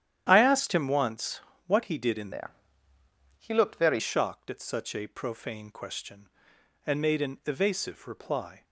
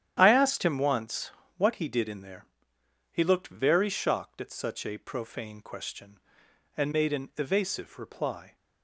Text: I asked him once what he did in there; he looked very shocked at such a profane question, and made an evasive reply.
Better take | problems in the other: second | starts louder than the rest; strong; until 1.3 s; 10.5 dB; strong in the second // pauses between "once" and "what"; slight; at 1.3 s; 0.28 s long; slight in the second // changes voice from "there" to "very"; from 2.3 to 3.9 s; 1.6 s long

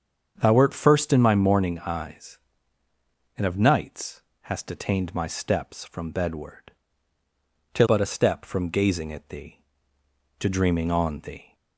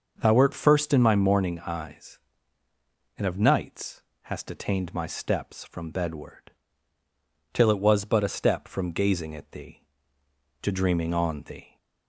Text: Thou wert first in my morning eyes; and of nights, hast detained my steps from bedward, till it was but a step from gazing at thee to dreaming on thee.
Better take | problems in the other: second | starts louder than the rest; strong; until 1.4 s; 7 dB; noticeable in the second // skips "it was"; at 7.8 s

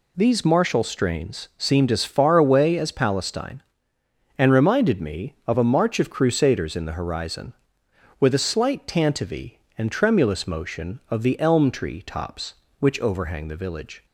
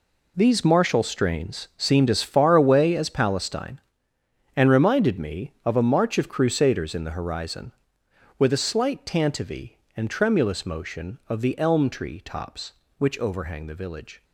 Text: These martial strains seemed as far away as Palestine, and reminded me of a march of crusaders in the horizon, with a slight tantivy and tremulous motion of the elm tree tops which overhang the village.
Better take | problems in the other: first | gets quieter; strong; throughout; 13 dB

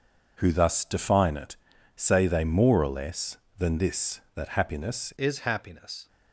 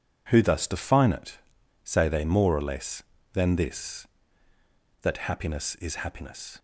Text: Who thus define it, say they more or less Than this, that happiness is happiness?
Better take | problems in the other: second | changes voice at "is"; from 5.1 s on; 0.9 s long

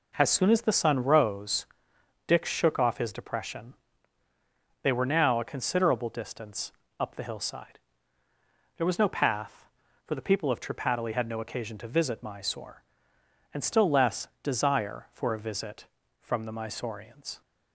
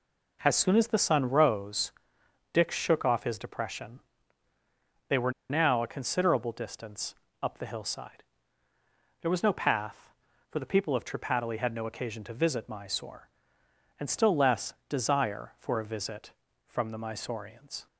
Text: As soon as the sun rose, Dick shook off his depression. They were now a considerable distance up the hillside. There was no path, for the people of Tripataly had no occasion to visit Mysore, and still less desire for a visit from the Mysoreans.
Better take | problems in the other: first | pauses between "were" and "now"; slight; at 5.3 s; 0.17 s long // pauses between "distance" and "up"; slight; at 7.1 s; 0.30 s long; slight in the first // pauses between "less" and "desire"; slight; at 14.7 s; 0.16 s long; slight in the first

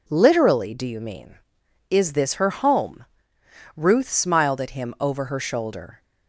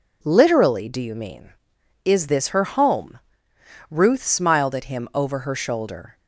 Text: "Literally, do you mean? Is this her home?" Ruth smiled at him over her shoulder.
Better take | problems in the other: neither | none

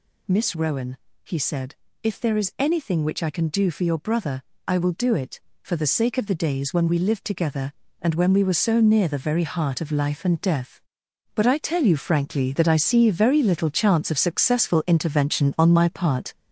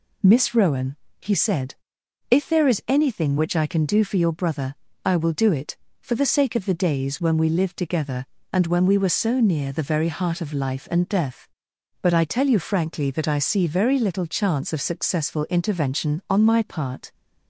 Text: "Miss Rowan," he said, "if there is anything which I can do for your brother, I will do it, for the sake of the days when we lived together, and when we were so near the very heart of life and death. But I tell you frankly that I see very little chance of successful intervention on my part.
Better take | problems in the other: second | gets louder; noticeable; throughout; 5.5 dB

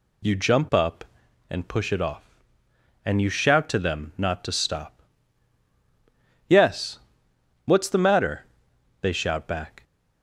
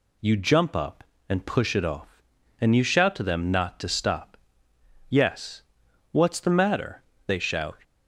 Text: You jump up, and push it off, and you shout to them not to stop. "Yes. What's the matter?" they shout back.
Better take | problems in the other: first | stops before "back"; at 7.8 s

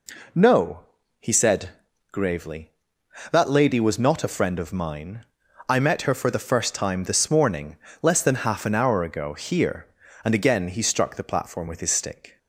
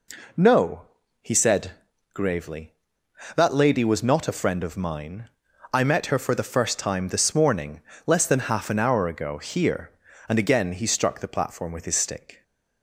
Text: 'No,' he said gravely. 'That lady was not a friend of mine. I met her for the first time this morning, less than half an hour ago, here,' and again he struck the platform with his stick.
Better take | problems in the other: neither | pauses between "said" and "gravely"; the same in both

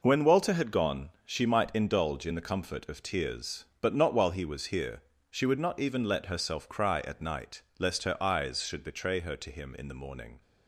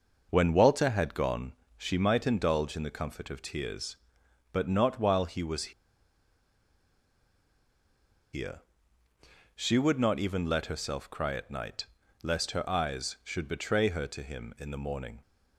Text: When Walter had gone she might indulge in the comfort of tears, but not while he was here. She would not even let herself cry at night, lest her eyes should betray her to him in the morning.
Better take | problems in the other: first | pauses between "gone" and "she"; slight; at 1.5 s; 0.22 s long // pauses between "was" and "here"; strong; at 5.7 s; 2.6 s long

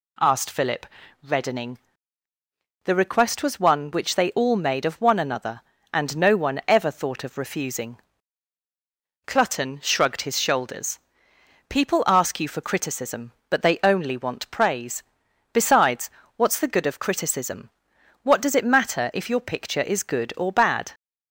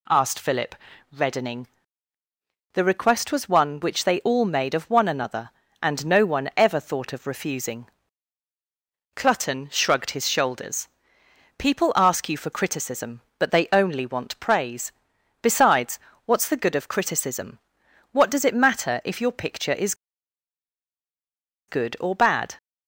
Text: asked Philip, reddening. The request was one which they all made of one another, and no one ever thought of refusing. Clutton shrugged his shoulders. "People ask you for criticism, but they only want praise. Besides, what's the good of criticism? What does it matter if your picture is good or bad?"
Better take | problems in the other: first | pauses between "is" and "good"; strong; at 19.9 s; 1.7 s long

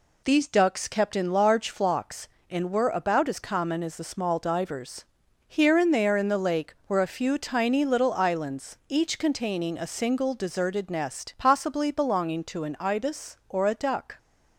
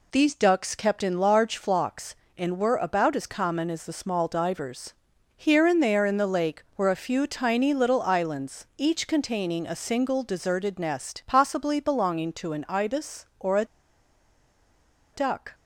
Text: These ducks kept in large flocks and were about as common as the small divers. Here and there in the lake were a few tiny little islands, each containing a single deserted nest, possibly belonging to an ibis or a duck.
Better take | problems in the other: first | pauses between "a" and "duck"; strong; at 13.6 s; 1.4 s long

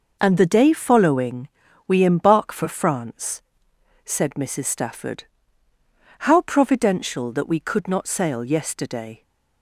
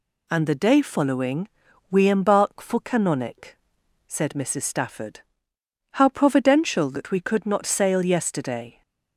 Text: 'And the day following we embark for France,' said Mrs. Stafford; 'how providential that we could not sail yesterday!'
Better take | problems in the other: first | pauses between "following" and "we"; at 1.4 s; 0.42 s long; also in the first // says "Canonic" for "France"; at 2.8 s

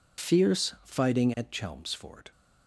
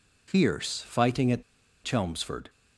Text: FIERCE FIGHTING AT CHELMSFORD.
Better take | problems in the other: first | pauses between "AT" and "CHELMSFORD"; at 1.4 s; 0.41 s long

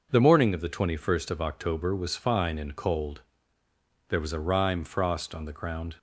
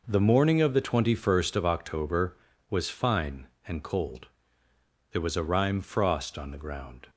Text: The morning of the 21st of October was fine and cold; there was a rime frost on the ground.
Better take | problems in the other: neither | none

